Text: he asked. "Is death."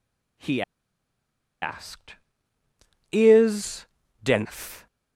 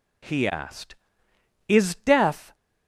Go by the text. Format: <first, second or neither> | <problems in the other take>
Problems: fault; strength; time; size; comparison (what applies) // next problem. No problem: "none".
second | pauses between "he" and "asked"; at 0.6 s; 0.99 s long // pauses between "Is" and "death"; at 3.8 s; 0.38 s long